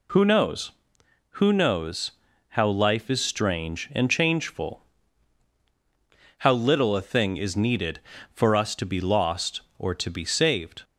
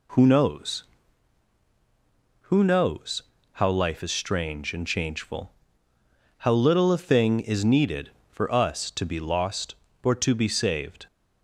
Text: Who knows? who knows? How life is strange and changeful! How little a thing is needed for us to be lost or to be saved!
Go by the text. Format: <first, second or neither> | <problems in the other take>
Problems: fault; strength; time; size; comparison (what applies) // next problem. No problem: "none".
neither | none